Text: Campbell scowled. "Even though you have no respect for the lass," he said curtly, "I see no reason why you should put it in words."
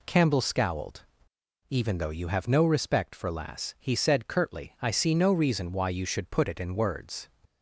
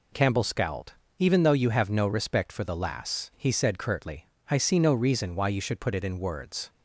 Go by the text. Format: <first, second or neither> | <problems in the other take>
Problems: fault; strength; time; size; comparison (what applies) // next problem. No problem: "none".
second | skips "the"; at 3.2 s